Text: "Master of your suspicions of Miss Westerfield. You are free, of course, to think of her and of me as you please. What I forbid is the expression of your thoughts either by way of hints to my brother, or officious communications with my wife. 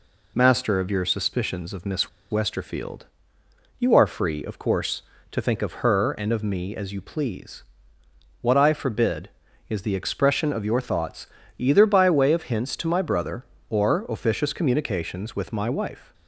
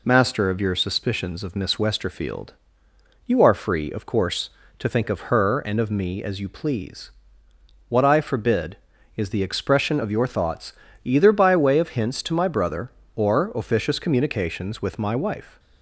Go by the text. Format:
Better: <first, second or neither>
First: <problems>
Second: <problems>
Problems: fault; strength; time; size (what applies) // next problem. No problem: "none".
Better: second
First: pauses between "Miss" and "Westerfield"; slight; at 2.0 s; 0.21 s long // pauses between "thoughts" and "either"; slight; at 11.2 s; 0.30 s long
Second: pauses between "thoughts" and "either"; slight; at 10.7 s; 0.30 s long